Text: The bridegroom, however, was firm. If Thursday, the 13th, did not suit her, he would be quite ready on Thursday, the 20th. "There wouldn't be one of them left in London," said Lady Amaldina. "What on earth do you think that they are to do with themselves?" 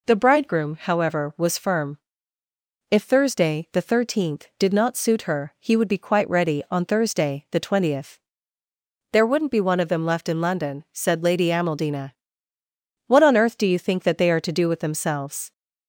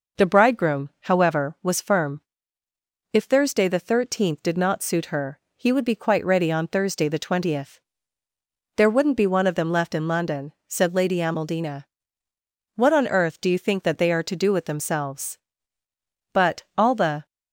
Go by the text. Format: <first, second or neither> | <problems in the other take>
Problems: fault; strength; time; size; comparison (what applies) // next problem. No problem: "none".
first | goes on to say "But all the"; noticeable; from 16.3 s on; 0.94 s long